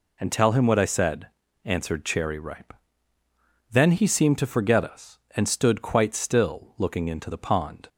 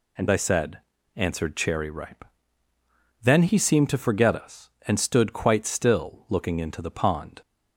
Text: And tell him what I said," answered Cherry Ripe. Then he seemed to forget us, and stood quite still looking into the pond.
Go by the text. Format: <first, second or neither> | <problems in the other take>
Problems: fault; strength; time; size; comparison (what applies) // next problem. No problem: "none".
first | skips "tell him what"; at 0.2 s